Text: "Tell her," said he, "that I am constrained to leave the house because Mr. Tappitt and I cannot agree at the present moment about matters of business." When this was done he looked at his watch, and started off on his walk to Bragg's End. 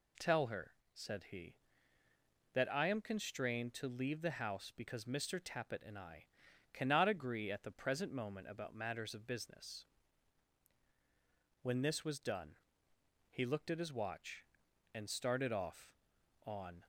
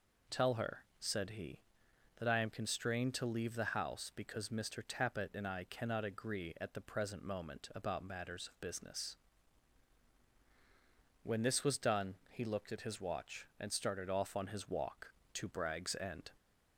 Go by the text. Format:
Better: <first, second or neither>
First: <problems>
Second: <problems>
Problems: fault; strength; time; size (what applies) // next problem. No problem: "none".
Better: second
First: pauses between "I" and "cannot"; at 6.2 s; 0.44 s long // pauses between "done" and "he"; noticeable; at 12.5 s; 0.74 s long // stops before "his walk to Bragg's End"; at 16.8 s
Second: none